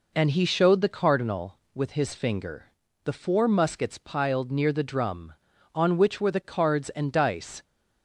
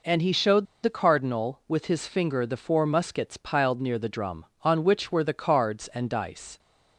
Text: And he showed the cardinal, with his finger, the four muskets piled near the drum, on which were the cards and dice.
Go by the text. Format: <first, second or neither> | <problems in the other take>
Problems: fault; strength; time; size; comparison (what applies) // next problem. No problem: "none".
first | pauses between "showed" and "the"; slight; at 0.6 s; 0.18 s long